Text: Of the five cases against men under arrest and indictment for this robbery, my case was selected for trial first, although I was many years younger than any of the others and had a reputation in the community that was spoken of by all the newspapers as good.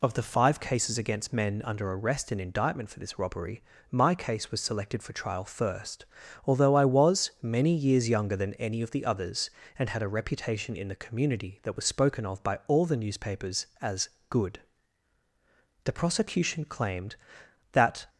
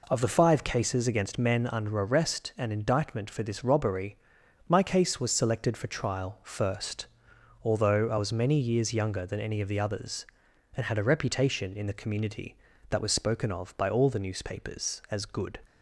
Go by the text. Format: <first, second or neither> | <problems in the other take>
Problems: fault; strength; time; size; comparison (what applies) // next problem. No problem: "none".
second | pauses between "as" and "good"; slight; at 14.0 s; 0.20 s long // goes on to say "The prosecution claimed that"; strong; from 15.8 s on; 2.2 s long